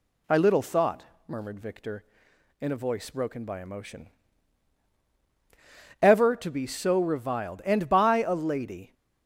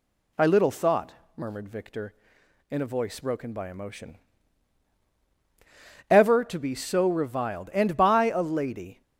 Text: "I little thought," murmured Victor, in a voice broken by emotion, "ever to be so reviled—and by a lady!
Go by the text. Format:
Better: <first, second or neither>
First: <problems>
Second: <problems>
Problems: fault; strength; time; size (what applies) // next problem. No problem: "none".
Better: neither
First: none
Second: none